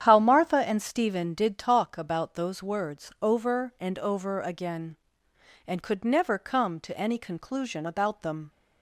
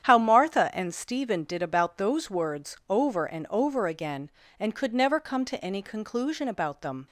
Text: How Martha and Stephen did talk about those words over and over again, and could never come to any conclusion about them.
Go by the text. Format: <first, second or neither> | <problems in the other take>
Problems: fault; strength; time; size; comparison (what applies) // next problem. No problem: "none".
first | starts louder than the rest; strong; until 1.1 s; 9.5 dB; strong in the first // skips "talk"; at 1.6 s